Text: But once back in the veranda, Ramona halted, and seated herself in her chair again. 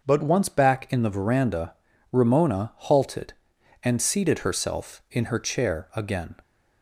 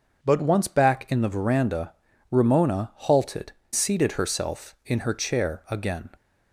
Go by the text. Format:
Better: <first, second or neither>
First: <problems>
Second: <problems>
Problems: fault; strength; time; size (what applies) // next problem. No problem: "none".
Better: first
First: none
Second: starts louder than the rest; until 1.2 s; 6.5 dB // skips "and"; at 3.6 s